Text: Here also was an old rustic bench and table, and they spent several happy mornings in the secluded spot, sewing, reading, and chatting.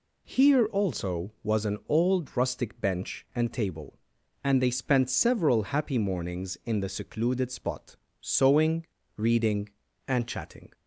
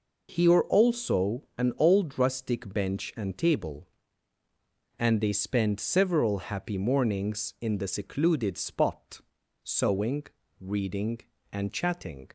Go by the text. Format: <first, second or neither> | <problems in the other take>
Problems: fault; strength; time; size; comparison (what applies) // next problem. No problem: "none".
first | skips "was"; at 1.4 s